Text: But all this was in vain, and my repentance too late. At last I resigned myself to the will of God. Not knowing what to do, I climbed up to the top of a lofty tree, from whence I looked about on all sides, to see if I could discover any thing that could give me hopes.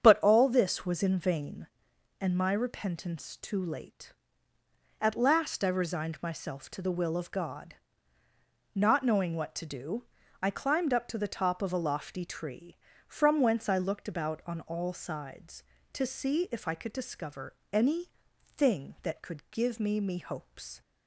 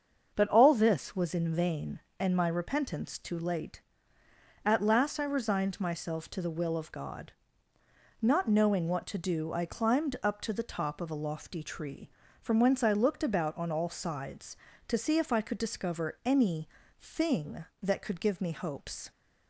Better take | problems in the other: second | starts louder than the rest; strong; until 1.0 s; 8 dB; also in the second // pauses between "discover" and "any"; slight; at 17.5 s; 0.18 s long // pauses between "any" and "thing"; noticeable; at 18.0 s; 0.50 s long; slight in the second // says "me" twice; at 20.0 s

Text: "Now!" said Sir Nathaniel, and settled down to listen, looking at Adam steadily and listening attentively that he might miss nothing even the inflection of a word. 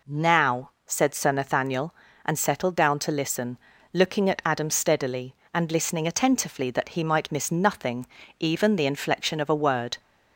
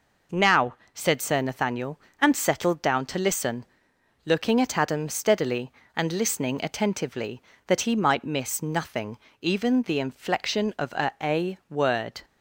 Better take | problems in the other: first | pauses between "nothing" and "even"; slight; at 9.1 s; 0.22 s long; slight in the first // says "a" twice; at 11.2 s

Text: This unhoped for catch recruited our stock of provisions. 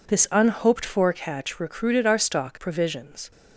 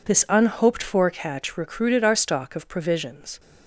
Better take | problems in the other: second | skips "of"; at 2.5 s

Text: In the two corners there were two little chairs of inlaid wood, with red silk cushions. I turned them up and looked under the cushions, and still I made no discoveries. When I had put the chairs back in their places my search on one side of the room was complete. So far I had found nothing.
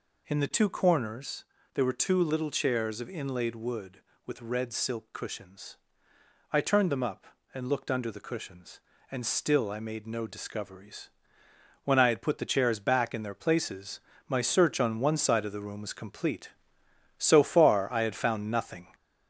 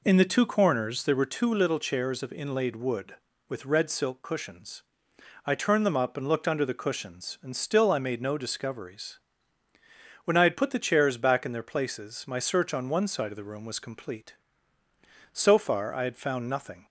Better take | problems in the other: second | gets louder; slight; throughout; 2.5 dB // pauses between "corners" and "there"; slight; at 1.4 s; 0.30 s long // pauses between "places" and "my"; slight; at 14.0 s; 0.26 s long

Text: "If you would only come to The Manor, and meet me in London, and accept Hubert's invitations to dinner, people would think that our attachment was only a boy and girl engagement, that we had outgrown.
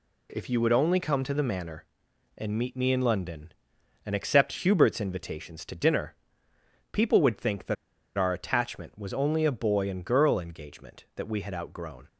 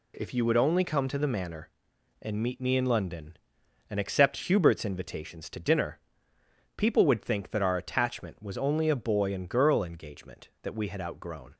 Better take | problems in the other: second | pauses between "that" and "our"; at 7.7 s; 0.41 s long

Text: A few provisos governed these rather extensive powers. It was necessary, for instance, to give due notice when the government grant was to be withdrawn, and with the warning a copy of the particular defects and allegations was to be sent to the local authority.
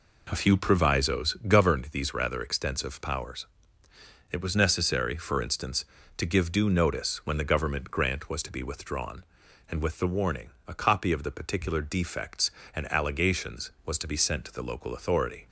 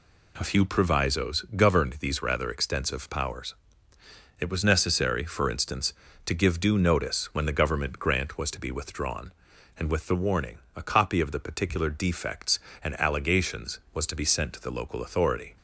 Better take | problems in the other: second | starts louder than the rest; until 1.7 s; 4 dB // pauses between "warning" and "a"; slight; at 10.4 s; 0.16 s long; slight in the second

